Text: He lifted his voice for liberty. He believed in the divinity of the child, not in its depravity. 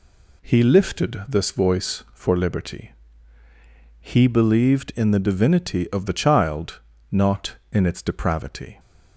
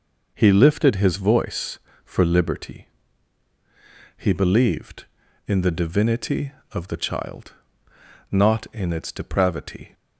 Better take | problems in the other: second | says "this" for "his"; at 1.2 s

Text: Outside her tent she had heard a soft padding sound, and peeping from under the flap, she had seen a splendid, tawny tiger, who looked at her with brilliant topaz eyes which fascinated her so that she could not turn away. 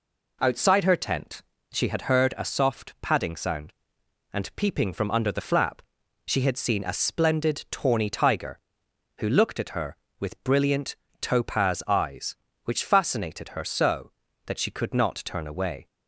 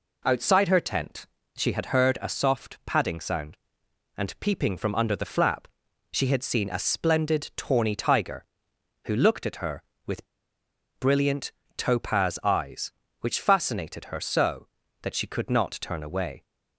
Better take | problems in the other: first | pauses between "tent" and "she"; slight; at 1.2 s; 0.28 s long; slight in the first // pauses between "with" and "brilliant"; noticeable; at 10.2 s; 0.73 s long // pauses between "brilliant" and "topaz"; slight; at 11.5 s; 0.24 s long; slight in the first

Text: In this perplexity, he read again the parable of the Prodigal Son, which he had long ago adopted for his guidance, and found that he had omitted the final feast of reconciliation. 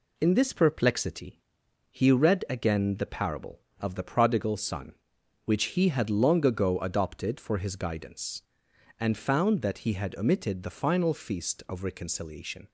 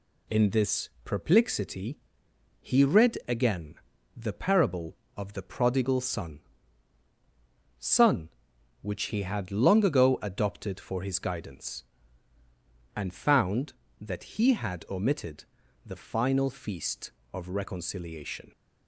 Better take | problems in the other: first | pauses between "this" and "perplexity"; slight; at 0.8 s; 0.16 s long // pauses between "again" and "the"; at 3.7 s; 0.38 s long // says "Son" twice; at 7.7 s // pauses between "omitted" and "the"; at 15.4 s; 0.40 s long

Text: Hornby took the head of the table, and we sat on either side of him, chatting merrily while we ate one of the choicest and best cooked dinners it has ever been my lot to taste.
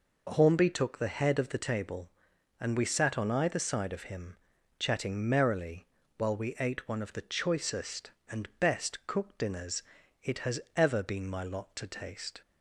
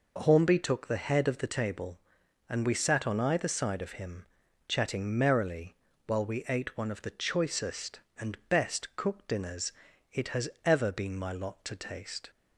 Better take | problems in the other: neither | pauses between "merrily" and "while"; slight; the same in both // pauses between "dinners" and "it"; the same in both // pauses between "has" and "ever"; slight; the same in both

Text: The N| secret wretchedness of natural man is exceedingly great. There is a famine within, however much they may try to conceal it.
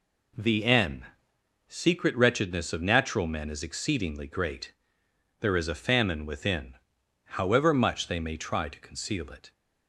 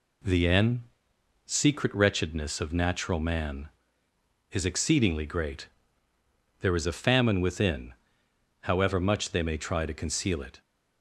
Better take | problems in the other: second | says "men" for "man"; at 3.2 s

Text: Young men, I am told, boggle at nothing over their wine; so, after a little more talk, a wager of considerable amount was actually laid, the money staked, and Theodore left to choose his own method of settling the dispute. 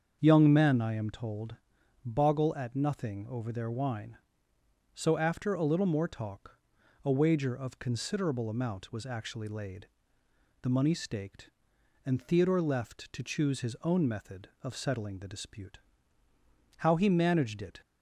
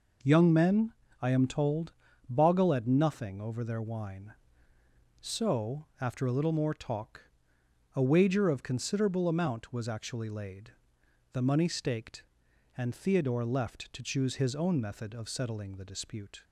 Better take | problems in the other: second | starts louder than the rest; until 1.2 s; 7 dB // goes on to say "How he managed it"; noticeable; from 16.7 s on; 1.0 s long

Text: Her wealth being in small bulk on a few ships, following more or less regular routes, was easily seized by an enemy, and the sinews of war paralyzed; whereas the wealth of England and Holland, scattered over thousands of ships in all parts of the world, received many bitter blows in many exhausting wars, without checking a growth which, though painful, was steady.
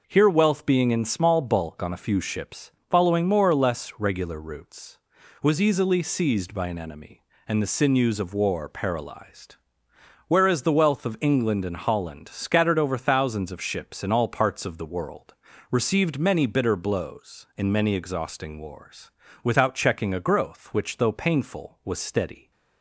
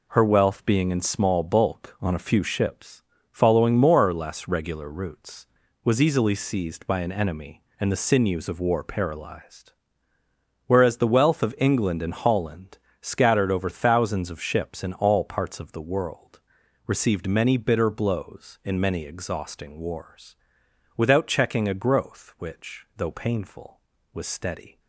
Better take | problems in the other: second | says "Here" for "Her"; at 0.0 s

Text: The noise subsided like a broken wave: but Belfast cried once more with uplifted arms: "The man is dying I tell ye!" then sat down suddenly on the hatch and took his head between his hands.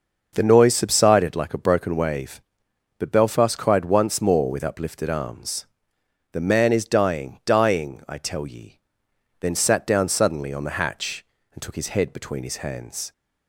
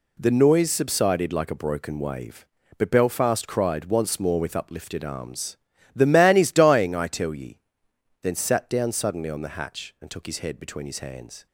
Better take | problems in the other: second | says "dying" twice; at 7.4 s

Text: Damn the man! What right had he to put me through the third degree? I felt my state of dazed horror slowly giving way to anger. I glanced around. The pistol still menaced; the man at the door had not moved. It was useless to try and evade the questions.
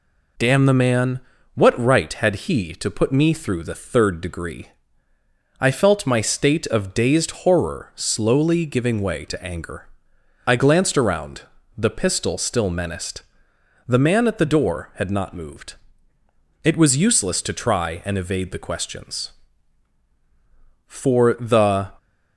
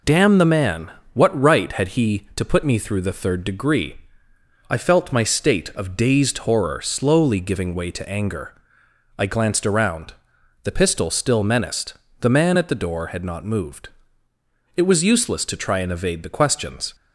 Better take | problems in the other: second | goes on to say "For the"; noticeable; from 20.8 s on; 1.0 s long

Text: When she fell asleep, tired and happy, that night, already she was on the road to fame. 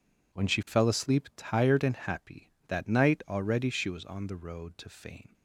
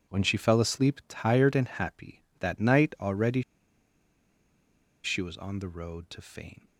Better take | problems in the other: first | pauses between "already" and "she"; strong; at 3.4 s; 1.6 s long

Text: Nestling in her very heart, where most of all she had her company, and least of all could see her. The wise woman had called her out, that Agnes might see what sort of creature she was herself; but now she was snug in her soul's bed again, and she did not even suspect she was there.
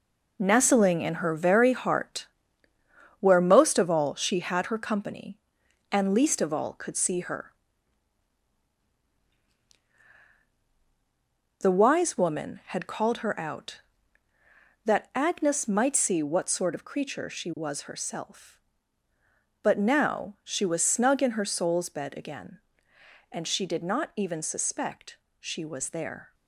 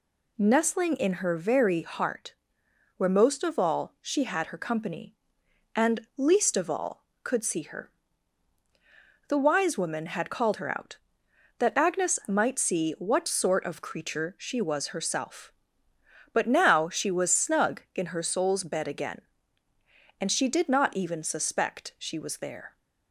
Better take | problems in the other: second | gets quieter; strong; throughout; 8.5 dB // pauses between "suspect" and "she"; slight; at 25.1 s; 0.24 s long

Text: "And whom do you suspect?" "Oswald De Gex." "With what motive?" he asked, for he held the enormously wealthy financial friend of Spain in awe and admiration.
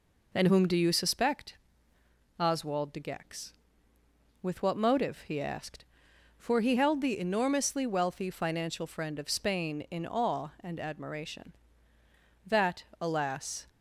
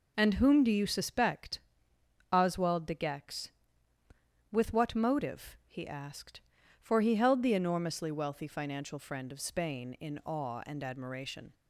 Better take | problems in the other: second | goes on to say "That alas"; noticeable; from 12.4 s on; 1.2 s long

